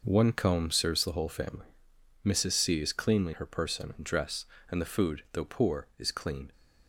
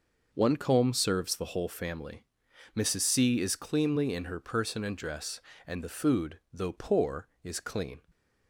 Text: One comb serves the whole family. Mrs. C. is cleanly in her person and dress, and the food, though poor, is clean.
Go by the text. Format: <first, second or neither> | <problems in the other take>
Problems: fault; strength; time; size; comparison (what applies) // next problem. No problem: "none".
second | skips "in"; at 3.3 s